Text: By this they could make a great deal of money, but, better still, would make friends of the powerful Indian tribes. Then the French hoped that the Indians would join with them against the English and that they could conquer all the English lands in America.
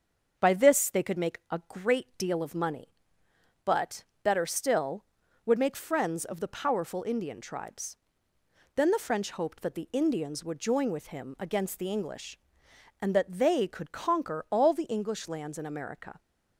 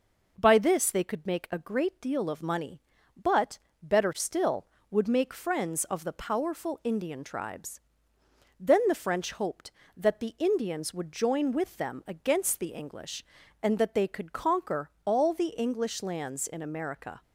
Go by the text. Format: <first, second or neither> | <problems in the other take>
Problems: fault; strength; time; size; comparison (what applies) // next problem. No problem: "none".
second | starts louder than the rest; until 1.3 s; 6.5 dB // says "him" for "them"; at 11.0 s